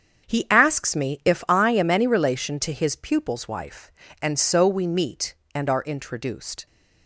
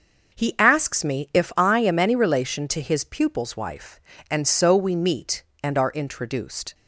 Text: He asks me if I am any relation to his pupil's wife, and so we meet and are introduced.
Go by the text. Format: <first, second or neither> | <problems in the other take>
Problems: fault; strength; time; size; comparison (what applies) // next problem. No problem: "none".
second | gets quieter; strong; throughout; 10.5 dB // starts louder than the rest; strong; until 1.3 s; 7.5 dB; noticeable in the second